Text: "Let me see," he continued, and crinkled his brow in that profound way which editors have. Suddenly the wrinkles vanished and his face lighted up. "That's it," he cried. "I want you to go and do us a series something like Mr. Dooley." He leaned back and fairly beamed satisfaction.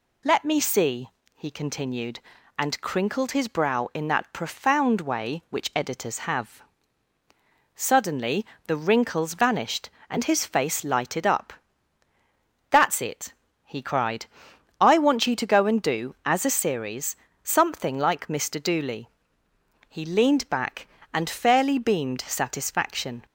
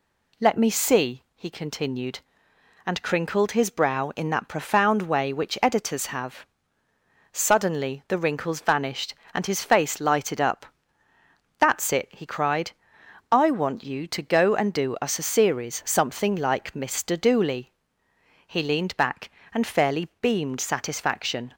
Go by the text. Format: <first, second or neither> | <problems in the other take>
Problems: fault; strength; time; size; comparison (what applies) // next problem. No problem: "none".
second | pauses between "Suddenly" and "the"; slight; at 8.4 s; 0.22 s long // says "as" for "us"; at 16.2 s // pauses between "series" and "something"; slight; at 17.1 s; 0.26 s long